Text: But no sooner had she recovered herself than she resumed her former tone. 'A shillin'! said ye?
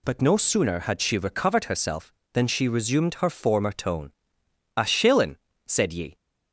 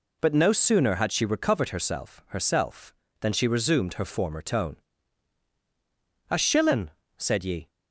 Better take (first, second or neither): first